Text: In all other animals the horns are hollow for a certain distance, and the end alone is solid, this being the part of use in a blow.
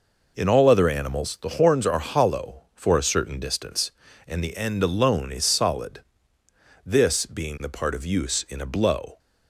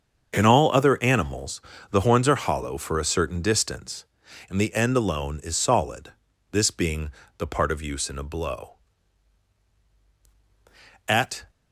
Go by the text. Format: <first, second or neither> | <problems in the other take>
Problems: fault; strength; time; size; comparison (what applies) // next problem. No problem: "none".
first | starts louder than the rest; until 1.3 s; 7 dB // pauses between "animals" and "the"; slight; at 1.6 s; 0.30 s long // pauses between "being" and "the"; slight; at 7.0 s; 0.28 s long // goes on to say "At"; slight; from 11.0 s on; 0.42 s long